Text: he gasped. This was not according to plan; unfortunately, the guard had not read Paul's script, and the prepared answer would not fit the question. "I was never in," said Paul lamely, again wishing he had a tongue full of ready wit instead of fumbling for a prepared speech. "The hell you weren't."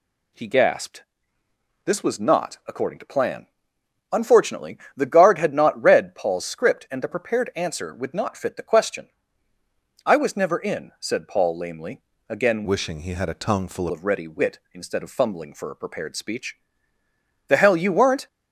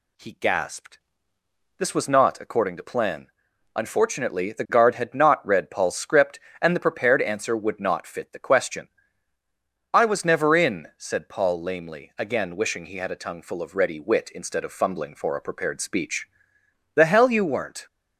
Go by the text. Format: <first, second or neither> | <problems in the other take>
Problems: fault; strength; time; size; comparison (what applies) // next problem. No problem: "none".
second | changes voice from "wishing" to "full"; from 12.6 to 13.8 s; 1.2 s long